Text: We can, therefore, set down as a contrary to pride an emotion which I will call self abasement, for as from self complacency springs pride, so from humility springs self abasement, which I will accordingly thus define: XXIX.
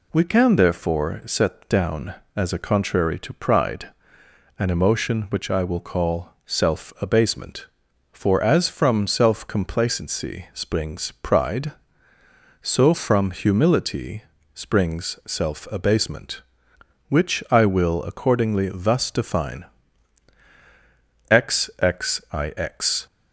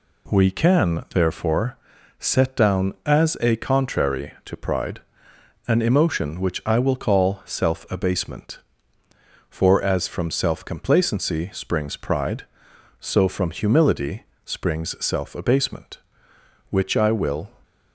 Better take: first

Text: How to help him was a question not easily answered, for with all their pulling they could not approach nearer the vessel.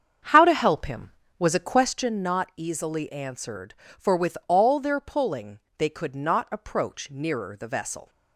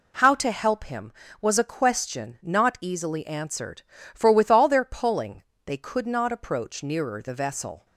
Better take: second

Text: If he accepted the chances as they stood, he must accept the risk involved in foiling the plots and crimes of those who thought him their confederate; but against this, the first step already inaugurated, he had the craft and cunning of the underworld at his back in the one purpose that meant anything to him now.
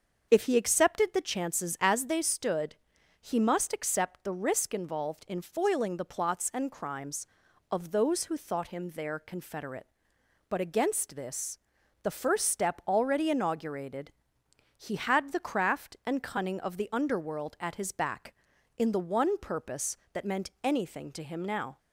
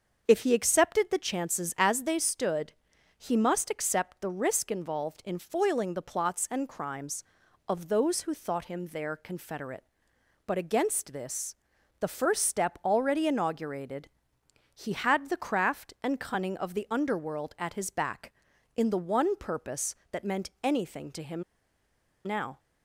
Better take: first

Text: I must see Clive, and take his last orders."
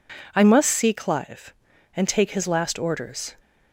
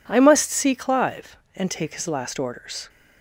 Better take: neither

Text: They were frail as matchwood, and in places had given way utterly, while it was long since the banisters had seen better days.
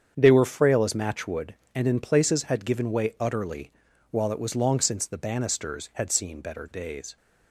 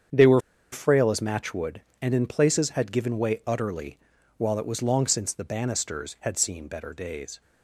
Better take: first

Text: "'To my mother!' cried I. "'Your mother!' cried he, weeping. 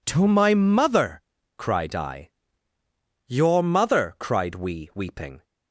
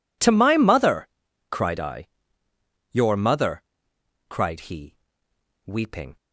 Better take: second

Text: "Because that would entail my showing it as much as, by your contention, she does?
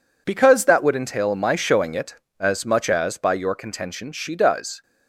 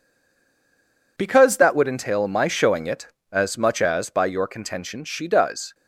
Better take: first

